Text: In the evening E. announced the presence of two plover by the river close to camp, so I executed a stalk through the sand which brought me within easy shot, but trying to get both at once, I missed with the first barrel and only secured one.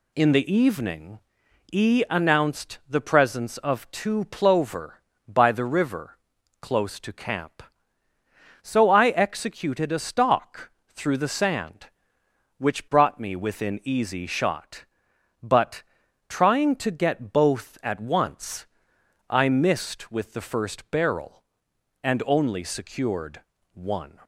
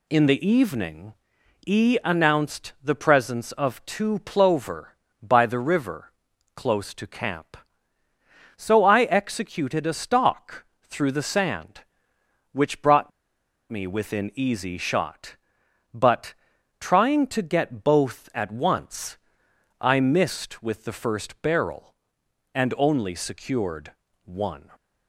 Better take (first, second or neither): first